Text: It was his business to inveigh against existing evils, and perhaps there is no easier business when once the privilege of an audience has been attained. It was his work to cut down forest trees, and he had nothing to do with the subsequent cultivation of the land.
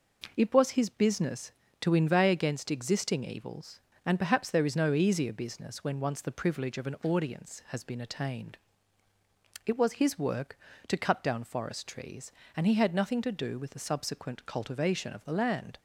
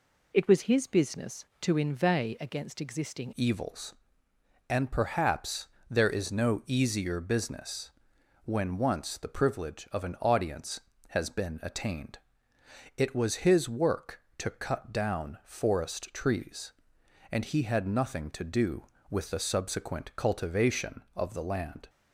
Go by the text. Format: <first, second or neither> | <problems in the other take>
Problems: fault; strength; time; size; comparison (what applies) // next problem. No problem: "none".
first | changes voice at "evils"; from 3.3 s on; 18.5 s long // pauses between "perhaps" and "there"; slight; at 5.6 s; 0.22 s long // pauses between "business" and "when"; noticeable; at 7.9 s; 0.54 s long